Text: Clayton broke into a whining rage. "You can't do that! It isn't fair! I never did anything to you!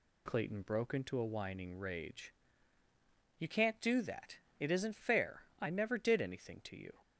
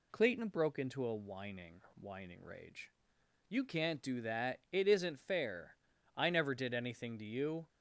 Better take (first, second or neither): first